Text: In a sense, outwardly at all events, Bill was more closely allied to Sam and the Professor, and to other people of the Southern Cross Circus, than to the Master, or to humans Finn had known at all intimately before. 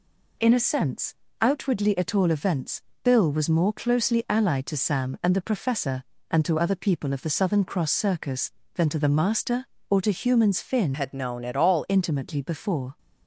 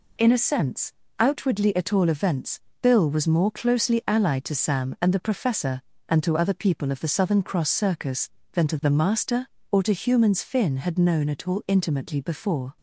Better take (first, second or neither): second